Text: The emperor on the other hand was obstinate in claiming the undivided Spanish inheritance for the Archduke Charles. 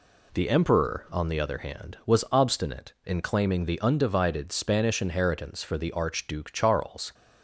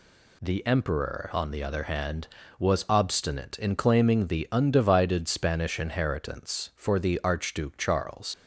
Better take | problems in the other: first | leaves "Charles" unfinished; at 8.3 s; 45 ms

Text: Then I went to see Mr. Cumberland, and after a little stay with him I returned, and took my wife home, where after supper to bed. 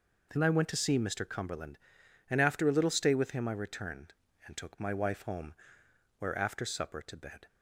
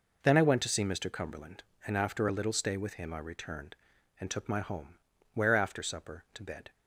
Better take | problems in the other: first | skips "wife"; at 4.5 s

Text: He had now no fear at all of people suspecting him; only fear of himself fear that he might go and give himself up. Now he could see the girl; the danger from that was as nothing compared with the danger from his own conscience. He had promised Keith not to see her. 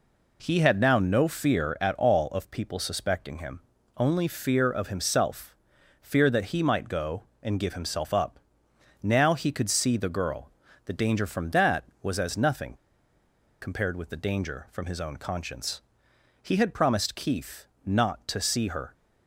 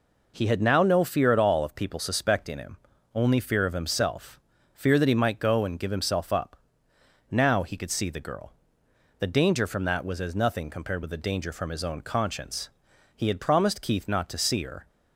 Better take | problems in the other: second | pauses between "himself" and "fear"; noticeable; at 5.5 s; 0.46 s long; slight in the second // pauses between "nothing" and "compared"; noticeable; at 12.7 s; 0.88 s long // pauses between "Keith" and "not"; slight; at 17.6 s; 0.18 s long

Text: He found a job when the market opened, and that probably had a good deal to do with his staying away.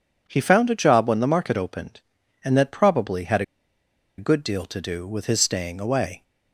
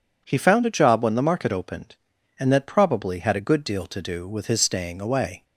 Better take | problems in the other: second | pauses between "had" and "a"; noticeable; at 3.4 s; 0.75 s long

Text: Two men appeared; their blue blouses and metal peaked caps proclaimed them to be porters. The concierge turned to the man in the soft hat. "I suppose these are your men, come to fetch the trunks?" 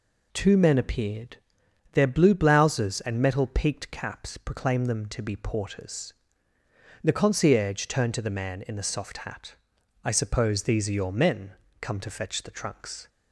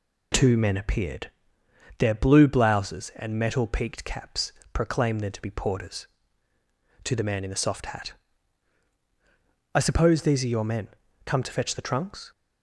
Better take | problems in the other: first | pauses between "caps" and "proclaimed"; slight; at 4.5 s; 0.22 s long // skips "The concierge turned"; at 6.5 s

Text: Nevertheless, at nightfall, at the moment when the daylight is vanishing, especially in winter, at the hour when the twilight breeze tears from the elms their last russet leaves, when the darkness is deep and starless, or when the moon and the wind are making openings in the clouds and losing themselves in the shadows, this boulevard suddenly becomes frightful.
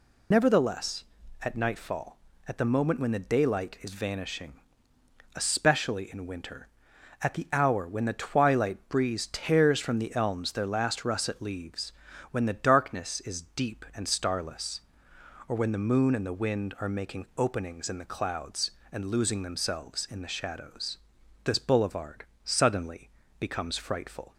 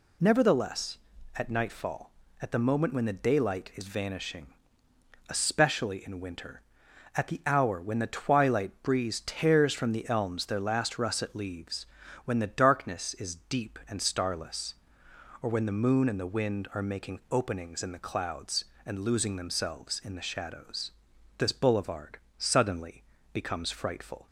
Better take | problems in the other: second | loses the start of "Nevertheless"; at 0.3 s; 35 ms // pauses between "boulevard" and "suddenly"; slight; at 22.2 s; 0.20 s long; slight in the second // pauses between "suddenly" and "becomes"; slight; at 23.0 s; 0.30 s long; slight in the second

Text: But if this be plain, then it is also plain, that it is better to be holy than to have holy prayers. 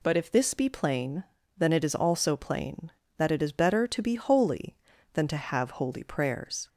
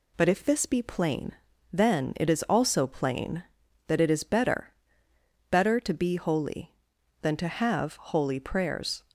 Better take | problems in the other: first | says "better" twice; at 5.5 s

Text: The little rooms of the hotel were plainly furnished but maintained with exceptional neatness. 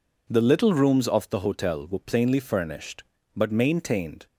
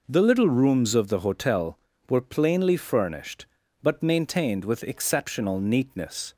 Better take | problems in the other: second | stops before "with exceptional neatness"; at 4.2 s

